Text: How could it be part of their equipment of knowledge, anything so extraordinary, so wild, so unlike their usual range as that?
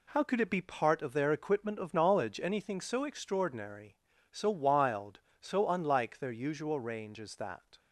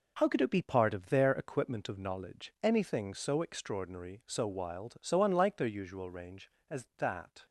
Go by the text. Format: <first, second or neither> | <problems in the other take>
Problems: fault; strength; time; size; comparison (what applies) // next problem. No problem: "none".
neither | none